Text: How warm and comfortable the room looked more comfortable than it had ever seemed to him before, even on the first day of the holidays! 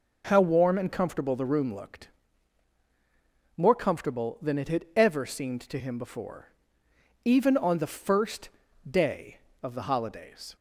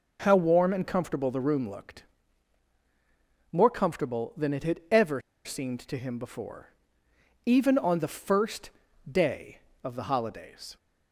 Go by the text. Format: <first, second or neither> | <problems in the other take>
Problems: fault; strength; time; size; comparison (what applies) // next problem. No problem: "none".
first | pauses between "looked" and "more"; strong; at 2.0 s; 1.4 s long; strong in the first // pauses between "ever" and "seemed"; slight; at 5.1 s; 0.26 s long // pauses between "first" and "day"; at 8.6 s; 0.42 s long; also in the first